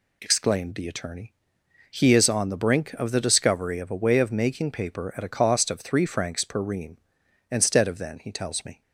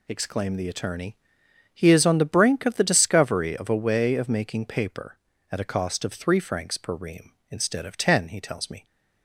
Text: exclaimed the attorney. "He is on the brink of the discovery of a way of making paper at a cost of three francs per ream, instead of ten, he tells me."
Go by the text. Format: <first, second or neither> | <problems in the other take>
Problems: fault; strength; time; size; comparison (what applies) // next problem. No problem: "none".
second | says "then" for "ten"; at 7.9 s